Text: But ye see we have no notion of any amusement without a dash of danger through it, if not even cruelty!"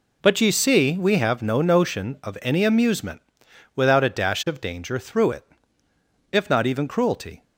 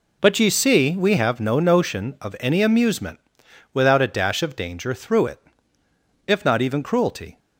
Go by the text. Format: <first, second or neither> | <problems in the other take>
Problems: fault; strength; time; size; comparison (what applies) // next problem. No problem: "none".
neither | pauses between "amusement" and "without"; noticeable; the same in both